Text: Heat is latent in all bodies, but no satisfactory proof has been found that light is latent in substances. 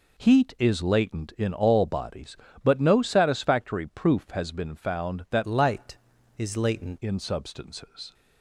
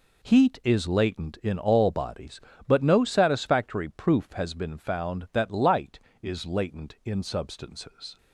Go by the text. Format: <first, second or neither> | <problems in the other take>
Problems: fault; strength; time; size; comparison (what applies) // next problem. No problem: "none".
second | changes voice from "light" to "latent"; from 5.4 to 6.9 s; 1.5 s long